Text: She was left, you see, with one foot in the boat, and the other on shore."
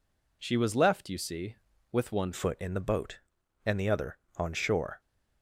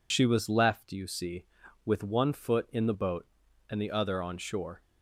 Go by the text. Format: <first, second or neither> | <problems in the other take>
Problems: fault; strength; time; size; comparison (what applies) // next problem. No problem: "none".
second | changes voice at "foot"; from 2.3 s on; 2.7 s long